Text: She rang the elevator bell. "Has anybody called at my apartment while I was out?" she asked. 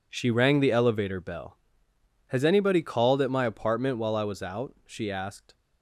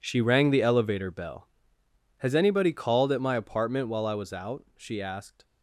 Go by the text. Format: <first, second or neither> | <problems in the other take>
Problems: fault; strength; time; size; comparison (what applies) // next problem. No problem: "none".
first | gets quieter; strong; throughout; 14.5 dB